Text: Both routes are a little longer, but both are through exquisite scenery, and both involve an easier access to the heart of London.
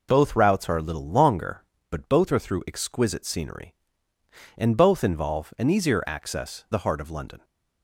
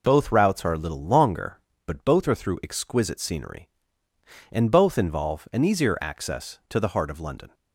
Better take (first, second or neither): second